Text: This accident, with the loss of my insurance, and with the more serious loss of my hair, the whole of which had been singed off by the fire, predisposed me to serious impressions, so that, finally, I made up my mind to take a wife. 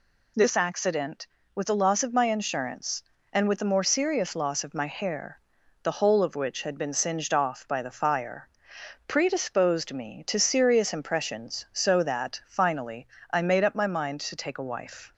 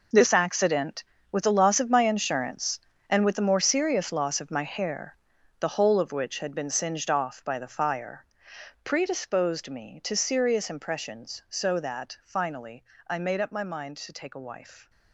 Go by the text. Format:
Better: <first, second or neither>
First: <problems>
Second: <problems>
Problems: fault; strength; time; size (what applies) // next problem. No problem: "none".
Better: first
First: none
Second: gets quieter; strong; throughout; 14 dB